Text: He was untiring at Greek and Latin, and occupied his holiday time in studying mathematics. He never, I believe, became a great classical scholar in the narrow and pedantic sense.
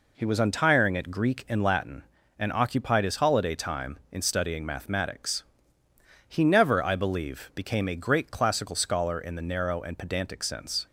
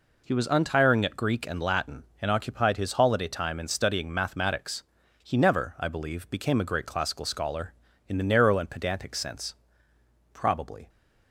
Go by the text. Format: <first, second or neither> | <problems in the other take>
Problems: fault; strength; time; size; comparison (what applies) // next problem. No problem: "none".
first | goes on to say "Probably"; from 10.3 s on; 0.56 s long